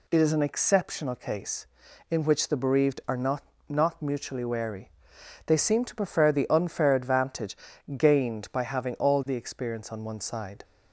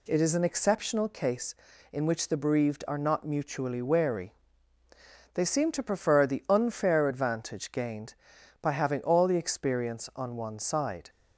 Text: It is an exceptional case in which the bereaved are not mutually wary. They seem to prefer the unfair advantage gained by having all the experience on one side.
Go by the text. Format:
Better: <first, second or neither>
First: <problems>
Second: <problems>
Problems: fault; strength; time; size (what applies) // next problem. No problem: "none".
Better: second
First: says "not" twice; at 3.6 s // pauses between "advantage" and "gained"; at 7.5 s; 0.40 s long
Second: none